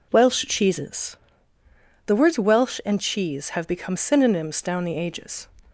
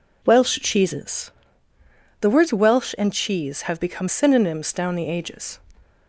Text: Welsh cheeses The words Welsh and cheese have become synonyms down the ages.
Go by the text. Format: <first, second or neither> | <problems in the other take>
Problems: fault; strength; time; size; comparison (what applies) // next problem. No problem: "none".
neither | pauses between "cheeses" and "The"; noticeable; the same in both